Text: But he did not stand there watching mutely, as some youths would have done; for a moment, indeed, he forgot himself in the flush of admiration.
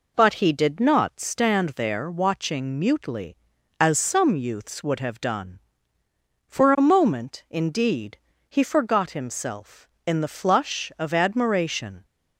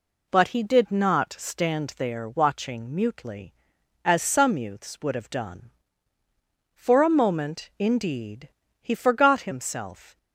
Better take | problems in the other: first | stops before "in the flush of admiration"; at 10.1 s

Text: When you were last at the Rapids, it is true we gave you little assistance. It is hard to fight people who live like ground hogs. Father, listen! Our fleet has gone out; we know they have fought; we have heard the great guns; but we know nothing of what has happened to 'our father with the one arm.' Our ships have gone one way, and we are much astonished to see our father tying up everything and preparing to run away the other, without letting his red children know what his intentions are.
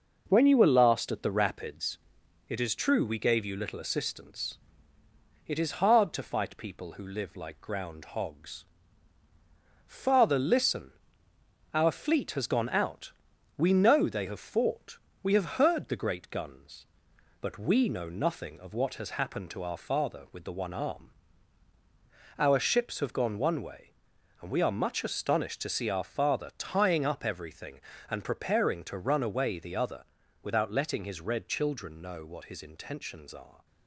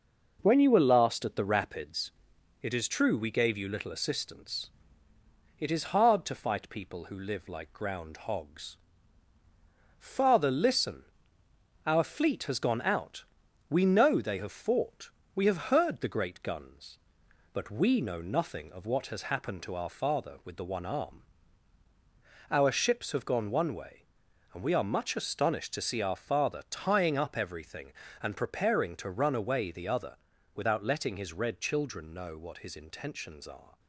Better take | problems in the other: neither | none

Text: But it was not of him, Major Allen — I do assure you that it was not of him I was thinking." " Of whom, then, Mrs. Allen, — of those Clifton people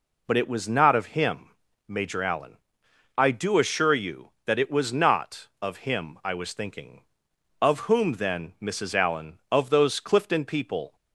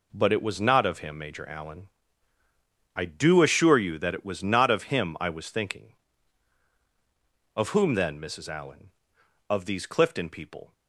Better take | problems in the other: first | says "these" for "those"; at 9.6 s

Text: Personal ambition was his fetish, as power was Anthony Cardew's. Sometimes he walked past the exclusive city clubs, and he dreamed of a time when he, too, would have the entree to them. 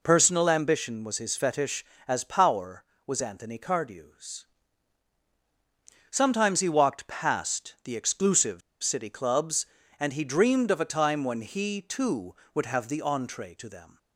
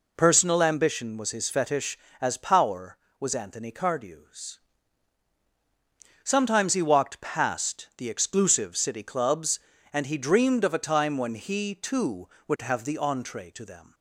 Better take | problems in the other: second | pauses between "exclusive" and "city"; slight; at 8.6 s; 0.22 s long

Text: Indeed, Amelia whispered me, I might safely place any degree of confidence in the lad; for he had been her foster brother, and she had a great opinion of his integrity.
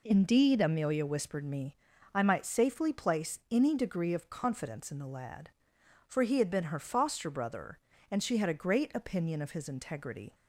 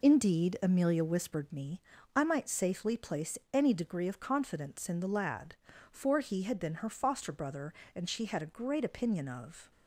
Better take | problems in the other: first | pauses between "place" and "any"; slight; at 3.3 s; 0.16 s long // stops before "his integrity"; at 9.7 s

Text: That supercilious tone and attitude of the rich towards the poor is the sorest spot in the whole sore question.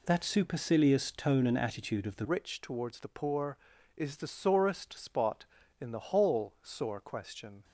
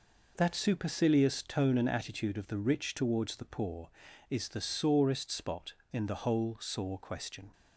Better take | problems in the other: second | changes voice at "rich"; from 2.2 s on; 5.4 s long

